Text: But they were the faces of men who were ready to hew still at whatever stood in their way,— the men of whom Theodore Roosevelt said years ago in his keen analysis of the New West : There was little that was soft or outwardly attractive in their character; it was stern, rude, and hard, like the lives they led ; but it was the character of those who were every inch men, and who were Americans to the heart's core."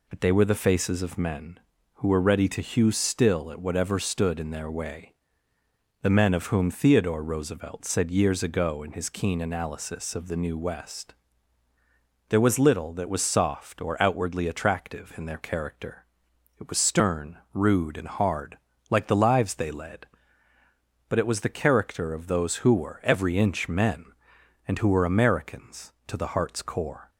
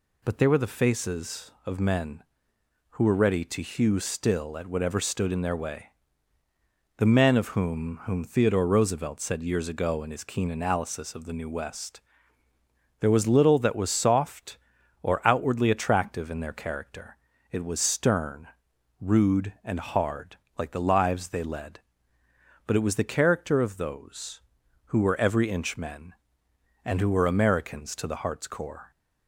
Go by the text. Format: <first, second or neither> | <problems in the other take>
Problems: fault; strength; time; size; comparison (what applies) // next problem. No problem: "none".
first | says "whom" twice; at 8.0 s